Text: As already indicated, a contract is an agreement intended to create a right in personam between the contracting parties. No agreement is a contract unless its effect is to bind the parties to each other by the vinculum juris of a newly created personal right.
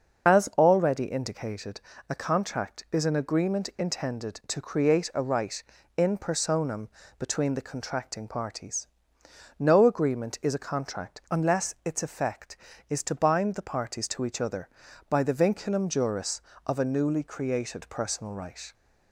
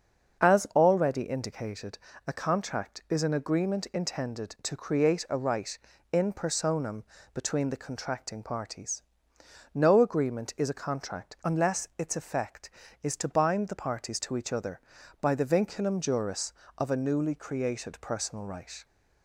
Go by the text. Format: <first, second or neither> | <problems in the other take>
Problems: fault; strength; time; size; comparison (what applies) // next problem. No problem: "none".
second | loses the start of "As"; at 0.2 s; 35 ms // starts louder than the rest; until 1.3 s; 6 dB; also in the second // pauses between "personam" and "between"; slight; at 6.8 s; 0.28 s long; slight in the second